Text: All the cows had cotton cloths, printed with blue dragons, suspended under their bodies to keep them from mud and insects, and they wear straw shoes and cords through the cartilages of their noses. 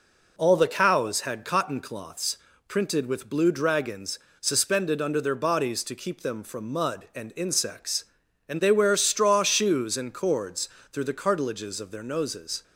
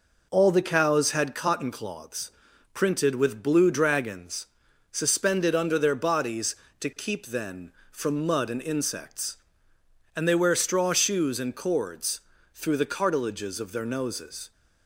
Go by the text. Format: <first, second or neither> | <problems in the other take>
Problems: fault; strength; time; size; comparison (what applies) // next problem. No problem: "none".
first | says "then" for "them"; at 7.2 s // pauses between "cords" and "through"; slight; at 12.2 s; 0.32 s long; slight in the first